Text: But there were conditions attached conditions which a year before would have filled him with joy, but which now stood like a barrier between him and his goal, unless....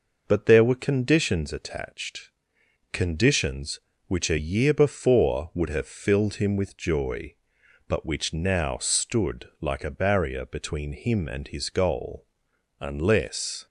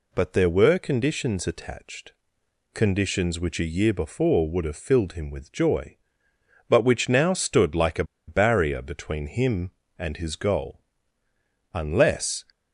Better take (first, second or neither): first